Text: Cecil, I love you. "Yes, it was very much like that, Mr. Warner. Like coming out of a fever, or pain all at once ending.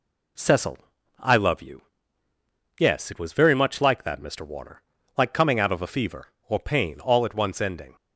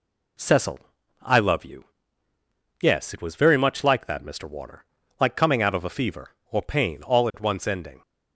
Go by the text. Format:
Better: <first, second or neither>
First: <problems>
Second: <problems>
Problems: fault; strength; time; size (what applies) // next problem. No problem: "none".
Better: neither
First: none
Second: none